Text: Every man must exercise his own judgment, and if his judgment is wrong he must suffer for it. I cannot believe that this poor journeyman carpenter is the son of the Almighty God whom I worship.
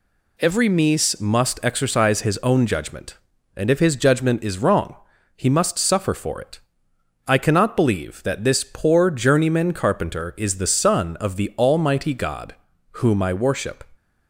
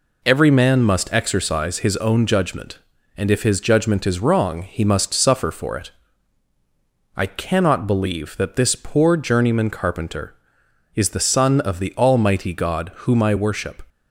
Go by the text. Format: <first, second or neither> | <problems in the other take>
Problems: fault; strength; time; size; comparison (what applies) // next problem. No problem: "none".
second | says "mies" for "man"; at 0.6 s // pauses between "wrong" and "he"; at 4.9 s; 0.40 s long // pauses between "God" and "whom"; slight; at 12.5 s; 0.36 s long